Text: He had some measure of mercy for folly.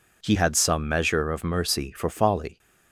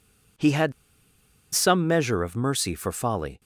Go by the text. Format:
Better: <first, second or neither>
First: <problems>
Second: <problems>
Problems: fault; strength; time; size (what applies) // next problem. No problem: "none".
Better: first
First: none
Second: pauses between "had" and "some"; noticeable; at 0.7 s; 0.81 s long